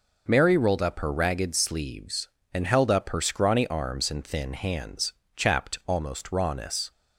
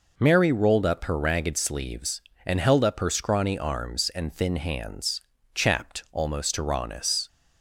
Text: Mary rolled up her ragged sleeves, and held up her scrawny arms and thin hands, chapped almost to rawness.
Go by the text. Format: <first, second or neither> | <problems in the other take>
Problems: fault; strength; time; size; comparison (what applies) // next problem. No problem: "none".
second | skips "to"; at 6.3 s